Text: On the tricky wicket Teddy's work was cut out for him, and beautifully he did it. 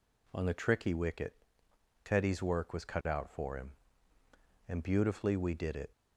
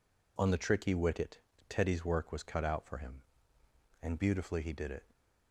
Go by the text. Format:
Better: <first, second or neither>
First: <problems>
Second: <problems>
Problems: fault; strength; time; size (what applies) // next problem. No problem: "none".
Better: second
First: pauses between "wicket" and "Teddy's"; noticeable; at 1.3 s; 0.70 s long // says "we" for "he"; at 5.3 s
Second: pauses between "wicket" and "Teddy's"; slight; at 1.3 s; 0.28 s long